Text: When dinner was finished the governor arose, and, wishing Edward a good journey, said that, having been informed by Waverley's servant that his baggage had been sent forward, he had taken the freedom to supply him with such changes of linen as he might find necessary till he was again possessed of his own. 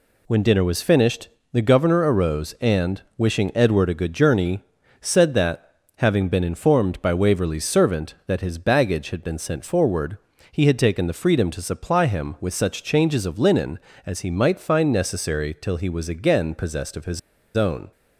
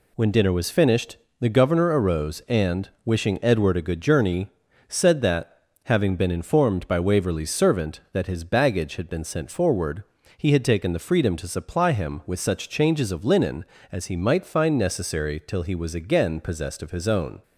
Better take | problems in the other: second | pauses between "finished" and "the"; slight; at 1.2 s; 0.24 s long; slight in the second // pauses between "his" and "own"; at 17.1 s; 0.37 s long

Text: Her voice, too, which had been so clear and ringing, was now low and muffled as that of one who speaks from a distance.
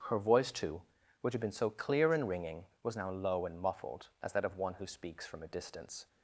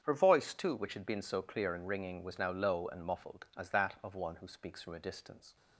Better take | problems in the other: neither | starts louder than the rest; strong; the same in both

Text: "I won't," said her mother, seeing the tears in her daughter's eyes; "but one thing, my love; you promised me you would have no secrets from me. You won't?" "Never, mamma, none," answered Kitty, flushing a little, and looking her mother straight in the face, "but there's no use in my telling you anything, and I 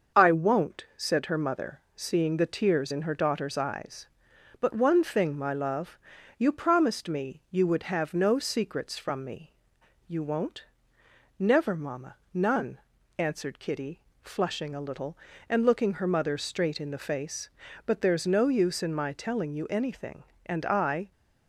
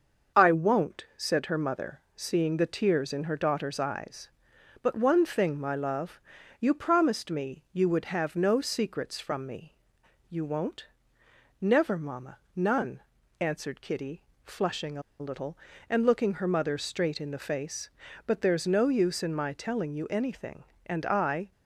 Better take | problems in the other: first | starts louder than the rest; until 1.4 s; 6.5 dB; also in the first // pauses between "a" and "little"; slight; at 15.0 s; 0.18 s long

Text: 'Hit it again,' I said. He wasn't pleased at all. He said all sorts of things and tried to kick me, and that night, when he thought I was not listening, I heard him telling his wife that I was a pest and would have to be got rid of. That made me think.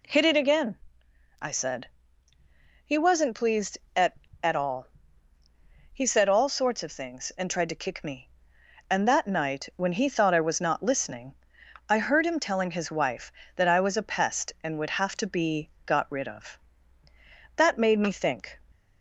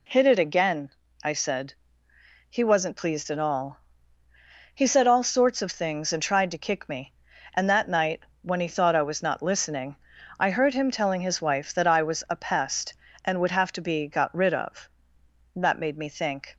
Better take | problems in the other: second | says "at" twice; at 4.4 s // pauses between "be" and "got"; slight; at 15.6 s; 0.18 s long

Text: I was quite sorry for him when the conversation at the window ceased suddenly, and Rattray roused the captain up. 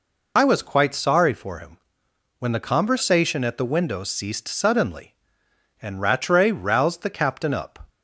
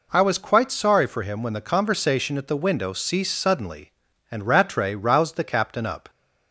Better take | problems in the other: second | loses the start of "I"; at 0.3 s; 45 ms // pauses between "him" and "when"; noticeable; at 1.7 s; 0.60 s long

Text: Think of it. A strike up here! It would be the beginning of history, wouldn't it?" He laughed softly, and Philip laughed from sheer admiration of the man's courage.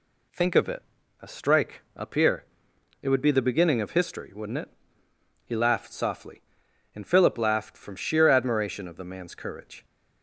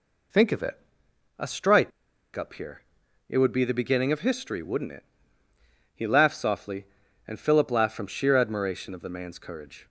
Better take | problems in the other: first | pauses between "strike" and "up"; at 1.9 s; 0.45 s long

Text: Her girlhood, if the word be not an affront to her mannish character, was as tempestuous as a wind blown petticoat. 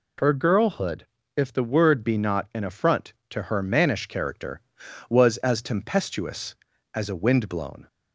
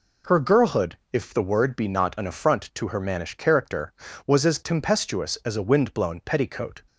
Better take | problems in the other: second | stops before "petticoat"; at 7.8 s

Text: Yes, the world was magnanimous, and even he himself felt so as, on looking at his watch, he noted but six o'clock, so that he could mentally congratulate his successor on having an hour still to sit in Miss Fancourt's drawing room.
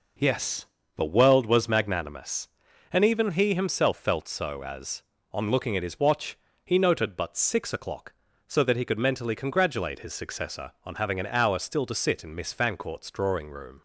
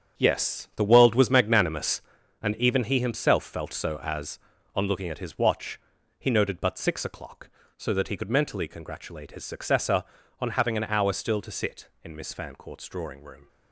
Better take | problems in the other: first | gets quieter; strong; throughout; 10 dB

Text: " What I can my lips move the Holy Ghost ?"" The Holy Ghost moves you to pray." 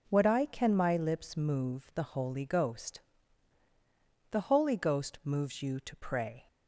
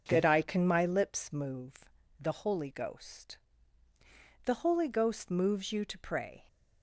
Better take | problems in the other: first | starts louder than the rest; strong; until 1.0 s; 7 dB // says "That" for "What"; at 0.0 s // pauses between "move" and "the"; slight; at 1.8 s; 0.32 s long

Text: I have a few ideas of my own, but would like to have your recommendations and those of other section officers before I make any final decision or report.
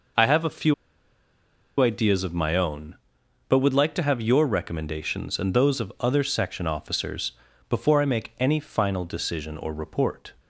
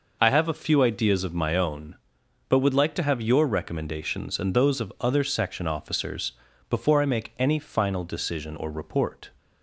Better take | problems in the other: second | pauses between "few" and "ideas"; at 0.7 s; 1.0 s long // pauses between "officers" and "before"; at 7.3 s; 0.38 s long; also in the second

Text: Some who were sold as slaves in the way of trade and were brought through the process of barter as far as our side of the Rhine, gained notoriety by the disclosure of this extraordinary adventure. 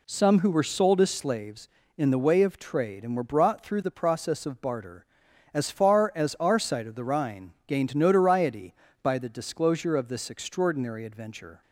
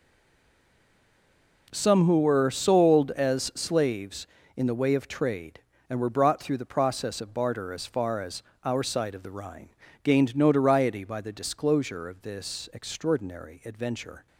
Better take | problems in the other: first | stays silent before the first word; noticeable; until 1.6 s; 1.6 s long // pauses between "as" and "our"; slight; at 8.4 s; 0.22 s long

